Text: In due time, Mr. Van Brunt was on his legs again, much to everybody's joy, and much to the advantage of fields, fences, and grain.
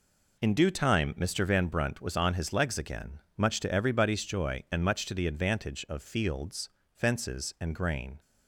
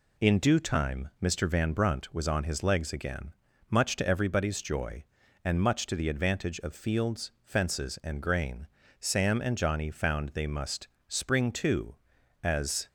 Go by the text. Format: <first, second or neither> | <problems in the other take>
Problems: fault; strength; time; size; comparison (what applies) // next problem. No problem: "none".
first | goes on to say "Sam and Johnny found they must spring to as"; strong; from 8.9 s on; 3.8 s long